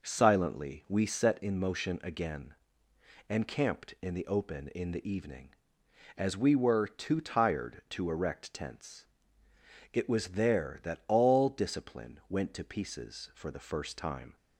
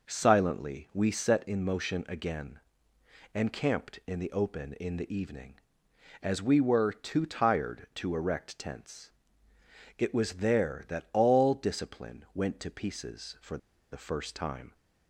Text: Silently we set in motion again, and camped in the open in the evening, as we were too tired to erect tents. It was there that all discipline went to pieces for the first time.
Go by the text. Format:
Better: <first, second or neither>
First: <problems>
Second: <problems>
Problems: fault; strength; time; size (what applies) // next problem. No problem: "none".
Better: first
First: none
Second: pauses between "for" and "the"; slight; at 13.5 s; 0.34 s long